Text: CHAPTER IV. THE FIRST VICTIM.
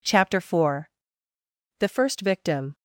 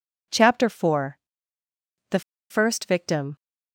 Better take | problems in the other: first | pauses between "THE" and "FIRST"; slight; at 2.2 s; 0.30 s long

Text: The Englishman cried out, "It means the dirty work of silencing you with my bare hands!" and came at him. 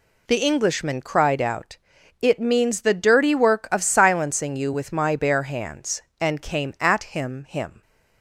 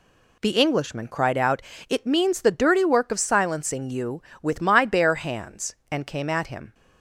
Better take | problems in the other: second | says "him" twice; at 7.4 s

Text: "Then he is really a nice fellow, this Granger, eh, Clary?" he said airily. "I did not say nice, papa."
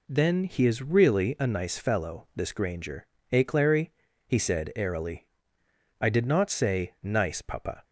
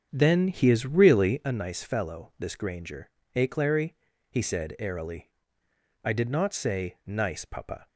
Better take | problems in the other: first | starts louder than the rest; strong; until 1.5 s; 7.5 dB

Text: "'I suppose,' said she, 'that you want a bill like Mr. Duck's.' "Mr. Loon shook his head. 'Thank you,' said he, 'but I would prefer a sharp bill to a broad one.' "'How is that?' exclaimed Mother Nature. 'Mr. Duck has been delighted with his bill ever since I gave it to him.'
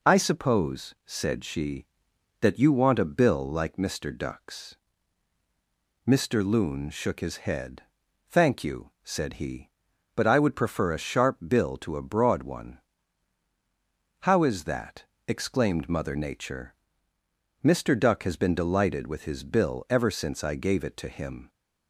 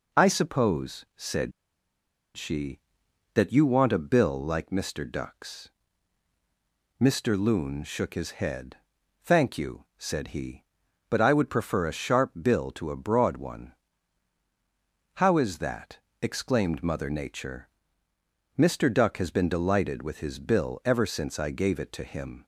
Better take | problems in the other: first | pauses between "said" and "she"; noticeable; at 1.5 s; 0.85 s long

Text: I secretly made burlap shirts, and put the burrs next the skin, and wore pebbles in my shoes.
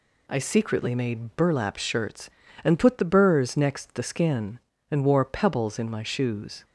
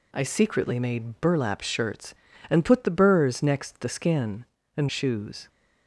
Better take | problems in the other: first | skips "wore pebbles in my"; at 4.8 s

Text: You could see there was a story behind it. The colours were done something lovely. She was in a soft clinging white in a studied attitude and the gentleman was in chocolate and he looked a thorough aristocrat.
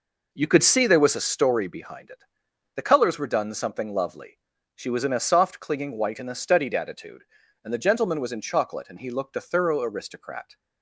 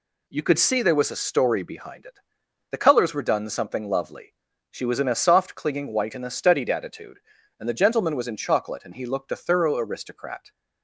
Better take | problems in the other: second | starts louder than the rest; noticeable; until 1.6 s; 5 dB

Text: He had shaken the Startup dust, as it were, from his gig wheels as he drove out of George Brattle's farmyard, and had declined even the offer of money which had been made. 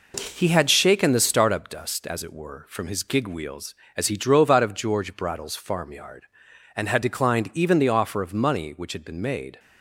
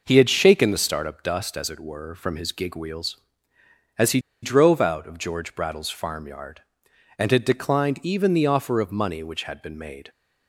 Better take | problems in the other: first | pauses between "he" and "drove"; slight; at 4.1 s; 0.24 s long

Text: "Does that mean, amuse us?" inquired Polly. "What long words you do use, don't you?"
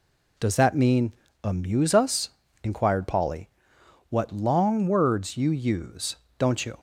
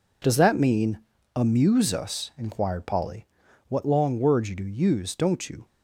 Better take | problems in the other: second | skips "do"; at 5.4 s

